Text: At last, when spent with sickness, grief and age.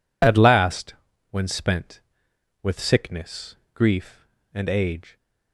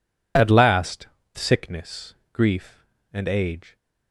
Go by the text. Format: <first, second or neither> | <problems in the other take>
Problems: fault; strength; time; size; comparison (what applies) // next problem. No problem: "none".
first | skips "when spent with"; at 1.2 s